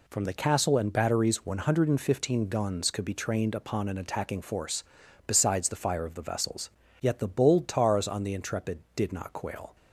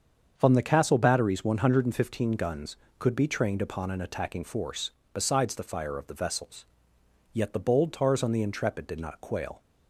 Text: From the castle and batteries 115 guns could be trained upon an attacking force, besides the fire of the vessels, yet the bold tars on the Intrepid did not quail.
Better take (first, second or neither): first